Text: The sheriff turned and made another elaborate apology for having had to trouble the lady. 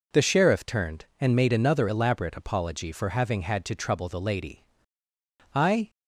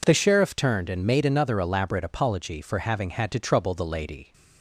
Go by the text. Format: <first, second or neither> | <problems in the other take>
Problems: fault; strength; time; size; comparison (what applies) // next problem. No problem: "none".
second | goes on to say "I"; slight; from 5.5 s on; 0.36 s long